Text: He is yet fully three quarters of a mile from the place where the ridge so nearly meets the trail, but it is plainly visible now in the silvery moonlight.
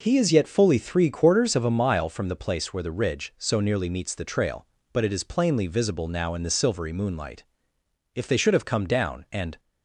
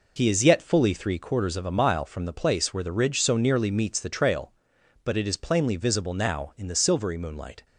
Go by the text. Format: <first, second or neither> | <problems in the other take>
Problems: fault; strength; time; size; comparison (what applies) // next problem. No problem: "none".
second | goes on to say "If they should have come down and"; from 8.1 s on; 1.4 s long